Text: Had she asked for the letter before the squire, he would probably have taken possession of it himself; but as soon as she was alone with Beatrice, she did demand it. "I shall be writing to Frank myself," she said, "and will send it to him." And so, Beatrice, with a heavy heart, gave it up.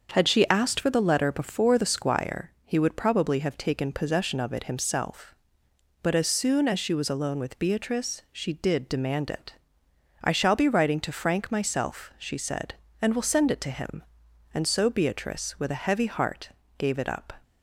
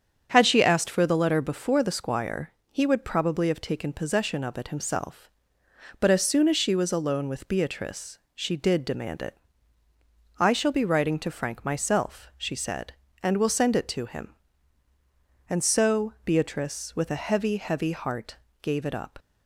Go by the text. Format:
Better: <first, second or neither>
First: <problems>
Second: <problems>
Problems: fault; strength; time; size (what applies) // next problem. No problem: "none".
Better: first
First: starts louder than the rest; until 1.1 s; 6.5 dB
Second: starts louder than the rest; strong; until 1.3 s; 8 dB // says "heavy" twice; at 17.5 s